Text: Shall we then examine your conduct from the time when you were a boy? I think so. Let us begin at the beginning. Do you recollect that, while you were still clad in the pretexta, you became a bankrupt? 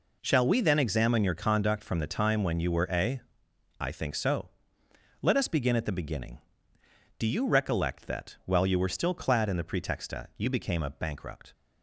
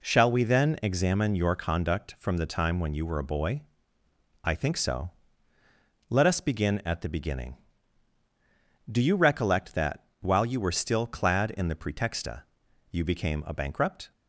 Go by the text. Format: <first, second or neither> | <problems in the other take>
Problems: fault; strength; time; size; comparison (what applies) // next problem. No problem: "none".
second | skips "boy"; at 3.4 s